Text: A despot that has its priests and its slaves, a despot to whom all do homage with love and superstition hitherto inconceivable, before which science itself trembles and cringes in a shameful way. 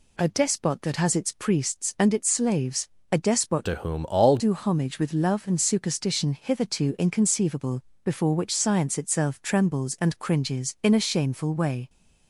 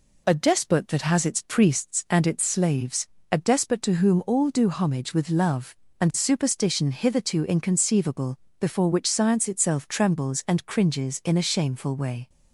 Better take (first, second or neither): second